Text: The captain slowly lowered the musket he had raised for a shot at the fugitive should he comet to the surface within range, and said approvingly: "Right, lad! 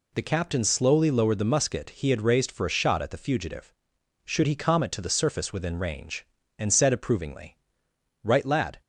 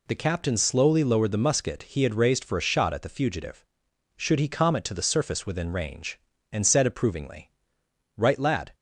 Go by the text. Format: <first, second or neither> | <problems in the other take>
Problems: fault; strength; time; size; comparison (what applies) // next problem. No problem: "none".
neither | none